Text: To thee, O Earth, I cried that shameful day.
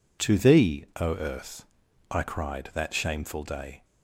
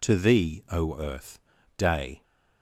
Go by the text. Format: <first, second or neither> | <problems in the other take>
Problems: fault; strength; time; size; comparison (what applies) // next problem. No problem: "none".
first | skips "I cried that shameful"; at 1.5 s